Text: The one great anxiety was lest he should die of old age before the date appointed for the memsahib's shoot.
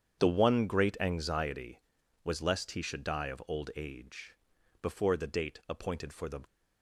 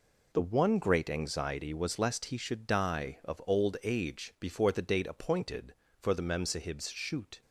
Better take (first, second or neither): second